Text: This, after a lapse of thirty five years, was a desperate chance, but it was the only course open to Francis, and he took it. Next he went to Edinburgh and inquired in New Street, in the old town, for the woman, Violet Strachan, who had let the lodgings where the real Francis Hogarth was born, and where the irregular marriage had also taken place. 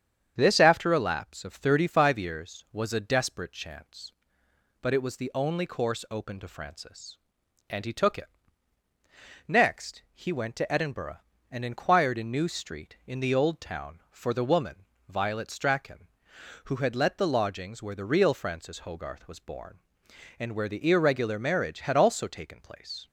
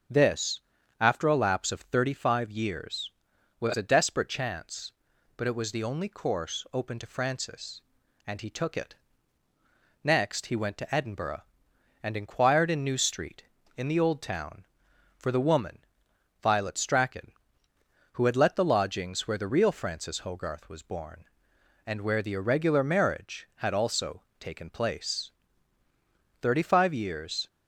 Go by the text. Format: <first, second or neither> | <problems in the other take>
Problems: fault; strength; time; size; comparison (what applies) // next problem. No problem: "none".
first | starts louder than the rest; strong; until 1.5 s; 7.5 dB; strong in the first // pauses between "also" and "taken"; slight; at 24.2 s; 0.20 s long // goes on to say "Thirty five years"; noticeable; from 26.4 s on; 1.0 s long